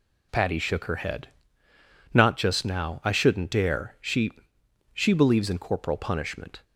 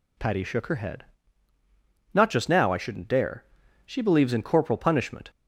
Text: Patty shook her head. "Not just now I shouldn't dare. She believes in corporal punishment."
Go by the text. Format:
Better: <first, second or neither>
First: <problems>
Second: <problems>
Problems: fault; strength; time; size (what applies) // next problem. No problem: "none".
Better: second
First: says "She" twice; at 4.9 s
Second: none